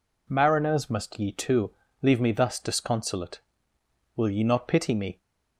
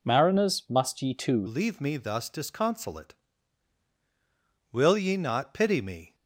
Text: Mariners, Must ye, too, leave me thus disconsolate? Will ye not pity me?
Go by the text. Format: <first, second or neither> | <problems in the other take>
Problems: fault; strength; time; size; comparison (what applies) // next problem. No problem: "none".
first | changes voice at "leave"; from 1.4 s on; 4.7 s long